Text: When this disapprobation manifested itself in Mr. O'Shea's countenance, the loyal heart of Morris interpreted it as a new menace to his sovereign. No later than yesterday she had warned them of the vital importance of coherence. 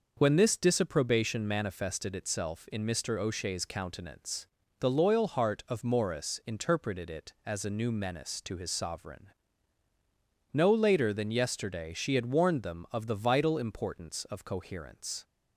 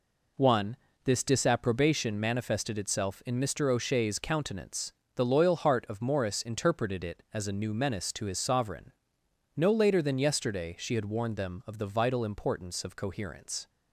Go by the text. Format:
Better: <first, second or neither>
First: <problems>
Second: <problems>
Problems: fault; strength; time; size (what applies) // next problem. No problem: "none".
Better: first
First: none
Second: says "One" for "When"; at 0.3 s